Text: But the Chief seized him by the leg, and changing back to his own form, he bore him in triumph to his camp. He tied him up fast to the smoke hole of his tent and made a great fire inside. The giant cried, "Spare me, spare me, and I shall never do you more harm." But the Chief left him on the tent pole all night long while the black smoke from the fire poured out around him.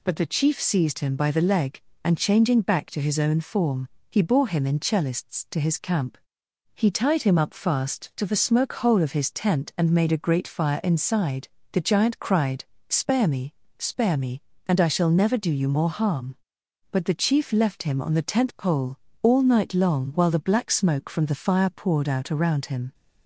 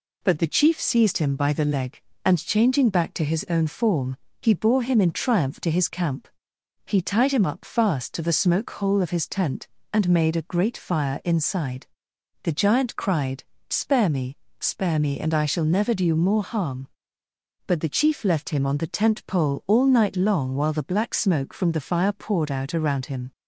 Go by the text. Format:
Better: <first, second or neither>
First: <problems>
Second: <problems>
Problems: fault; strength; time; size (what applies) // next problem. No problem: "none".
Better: second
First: says "cellists" for "triumph"; at 4.7 s // pauses between "pole" and "all"; slight; at 18.9 s; 0.24 s long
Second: none